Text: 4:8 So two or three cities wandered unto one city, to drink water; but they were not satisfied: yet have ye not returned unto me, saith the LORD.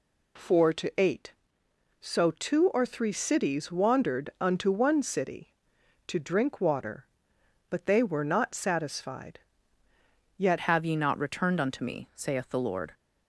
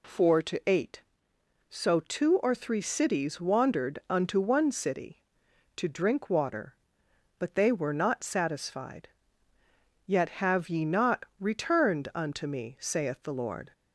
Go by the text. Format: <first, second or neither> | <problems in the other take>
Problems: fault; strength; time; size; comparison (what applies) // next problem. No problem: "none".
second | changes voice at "have"; from 10.5 s on; 2.4 s long